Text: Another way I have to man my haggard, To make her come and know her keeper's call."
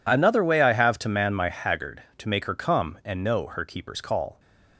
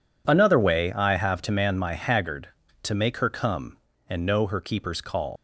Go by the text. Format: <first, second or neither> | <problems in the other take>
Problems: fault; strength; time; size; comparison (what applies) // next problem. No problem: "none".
first | leaves "call" unfinished; at 5.3 s; 105 ms